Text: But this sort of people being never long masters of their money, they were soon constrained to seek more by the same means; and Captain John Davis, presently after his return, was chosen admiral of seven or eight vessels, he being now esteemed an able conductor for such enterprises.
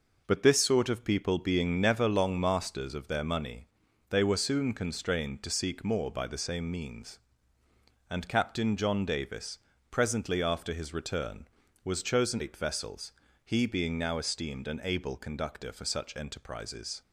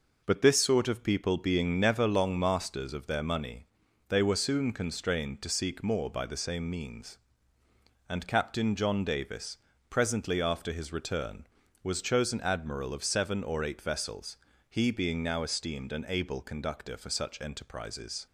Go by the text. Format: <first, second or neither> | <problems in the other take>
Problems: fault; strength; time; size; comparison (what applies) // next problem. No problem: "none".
second | skips "admiral of seven or"; at 12.3 s